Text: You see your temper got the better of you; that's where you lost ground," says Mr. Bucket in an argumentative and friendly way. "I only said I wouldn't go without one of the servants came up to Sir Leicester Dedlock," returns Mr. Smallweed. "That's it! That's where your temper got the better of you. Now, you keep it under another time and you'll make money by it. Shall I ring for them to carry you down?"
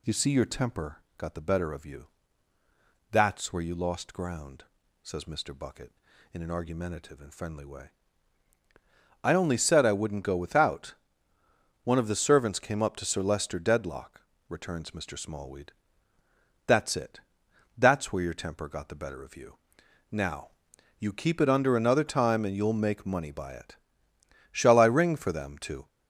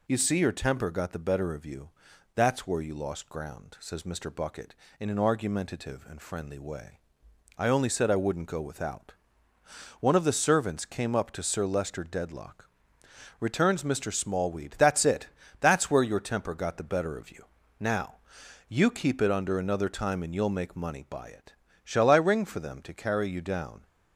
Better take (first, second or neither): second